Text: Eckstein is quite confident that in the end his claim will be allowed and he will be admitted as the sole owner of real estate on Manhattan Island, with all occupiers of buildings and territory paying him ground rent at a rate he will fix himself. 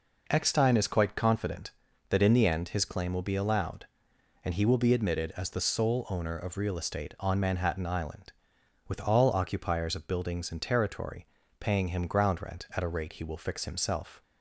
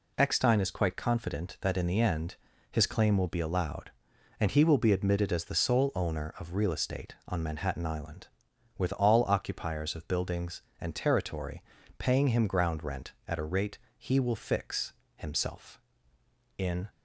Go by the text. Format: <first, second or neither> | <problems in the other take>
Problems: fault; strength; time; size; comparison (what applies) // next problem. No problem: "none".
first | pauses between "end" and "his"; slight; at 2.3 s; 0.34 s long // pauses between "territory" and "paying"; slight; at 11.6 s; 0.36 s long; slight in the first // pauses between "rate" and "he"; slight; at 13.7 s; 0.20 s long // pauses between "fix" and "himself"; slight; at 14.9 s; 0.24 s long // goes on to say "In"; slight; from 16.5 s on; 0.30 s long